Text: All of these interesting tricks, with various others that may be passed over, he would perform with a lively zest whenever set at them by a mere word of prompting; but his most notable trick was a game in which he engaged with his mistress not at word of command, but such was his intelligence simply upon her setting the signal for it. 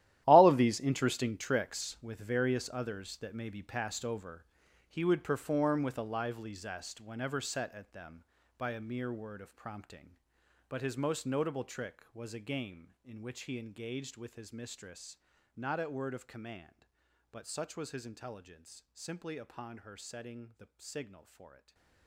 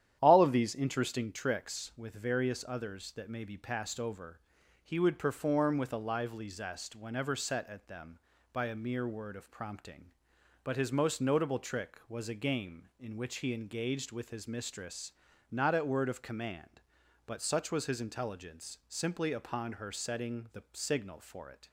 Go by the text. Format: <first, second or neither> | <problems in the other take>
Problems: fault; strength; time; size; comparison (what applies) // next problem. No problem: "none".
second | gets quieter; strong; throughout; 15 dB // starts louder than the rest; strong; until 1.2 s; 13.5 dB; strong in the second // pauses between "mistress" and "not"; at 15.1 s; 0.40 s long; also in the second // stays silent after the last word; slight; from 21.5 s on; 0.5 s long